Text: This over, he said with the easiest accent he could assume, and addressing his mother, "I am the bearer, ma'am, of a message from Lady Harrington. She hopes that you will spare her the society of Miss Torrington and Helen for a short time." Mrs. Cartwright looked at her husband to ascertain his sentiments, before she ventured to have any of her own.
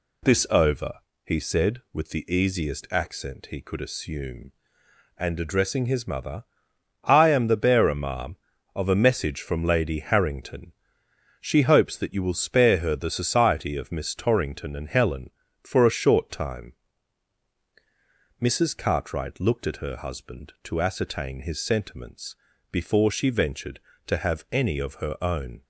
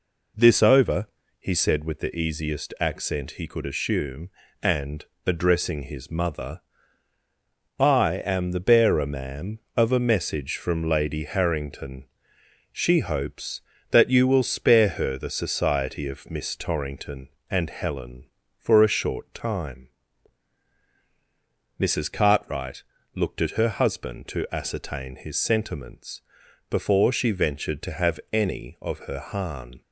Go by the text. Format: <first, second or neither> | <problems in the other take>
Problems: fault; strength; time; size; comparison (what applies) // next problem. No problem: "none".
first | pauses between "and" and "addressing"; slight; at 5.0 s; 0.20 s long // pauses between "Cartwright" and "looked"; slight; at 22.8 s; 0.32 s long // says "harn" for "own"; at 29.1 s